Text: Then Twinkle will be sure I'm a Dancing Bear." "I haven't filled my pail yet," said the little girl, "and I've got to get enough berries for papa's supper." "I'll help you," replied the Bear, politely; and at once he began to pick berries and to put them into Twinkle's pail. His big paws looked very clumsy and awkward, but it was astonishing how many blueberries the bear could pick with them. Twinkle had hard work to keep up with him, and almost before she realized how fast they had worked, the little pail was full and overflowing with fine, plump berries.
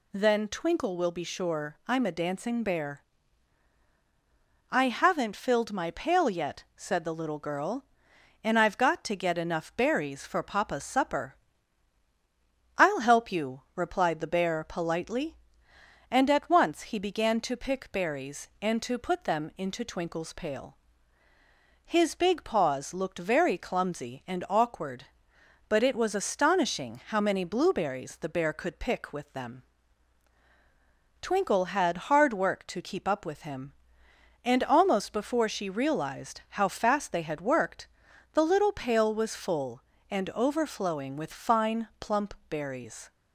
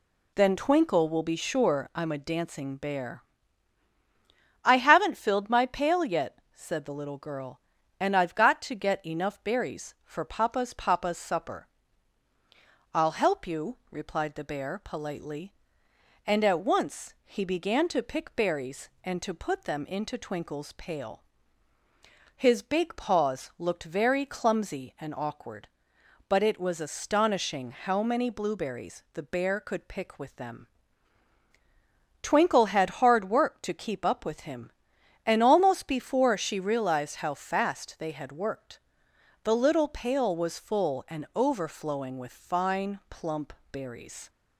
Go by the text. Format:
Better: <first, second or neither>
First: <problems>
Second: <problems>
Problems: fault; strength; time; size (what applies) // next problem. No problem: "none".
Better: first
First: pauses between "plump" and "berries"; slight; at 42.3 s; 0.16 s long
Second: says "papa's" twice; at 10.7 s // pauses between "plump" and "berries"; slight; at 43.5 s; 0.18 s long